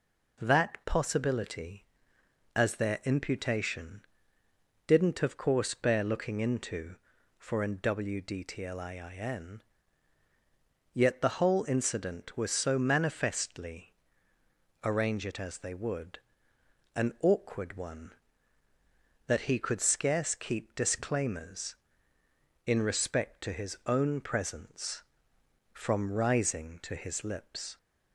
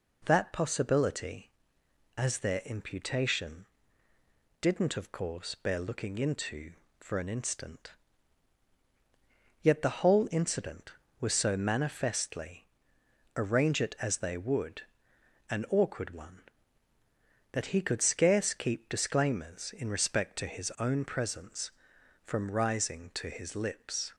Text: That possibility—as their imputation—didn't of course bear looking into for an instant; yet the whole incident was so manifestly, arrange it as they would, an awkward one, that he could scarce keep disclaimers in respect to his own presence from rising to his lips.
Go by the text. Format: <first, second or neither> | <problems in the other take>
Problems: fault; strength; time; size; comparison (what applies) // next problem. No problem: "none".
second | says "wdtliin" for "instant"; at 7.7 s